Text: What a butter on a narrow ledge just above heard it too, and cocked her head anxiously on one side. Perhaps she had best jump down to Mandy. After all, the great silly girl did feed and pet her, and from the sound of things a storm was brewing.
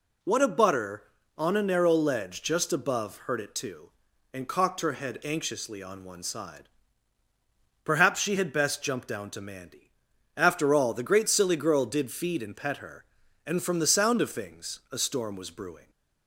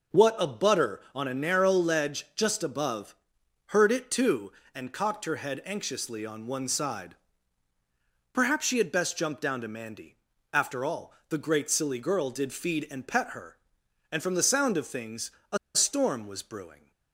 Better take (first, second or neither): first